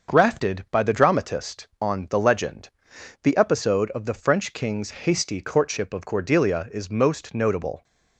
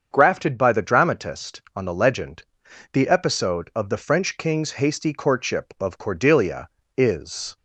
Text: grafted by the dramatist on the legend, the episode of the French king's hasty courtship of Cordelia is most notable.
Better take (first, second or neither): first